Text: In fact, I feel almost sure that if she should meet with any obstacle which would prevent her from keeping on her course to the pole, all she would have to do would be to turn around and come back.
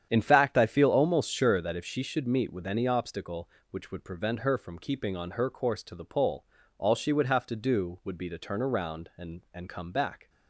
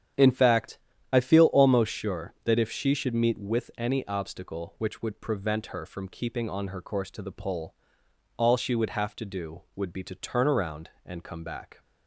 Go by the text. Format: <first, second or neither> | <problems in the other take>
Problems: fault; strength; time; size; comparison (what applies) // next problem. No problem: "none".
second | starts louder than the rest; strong; until 1.1 s; 9 dB; strong in the second // says "and" twice; at 9.5 s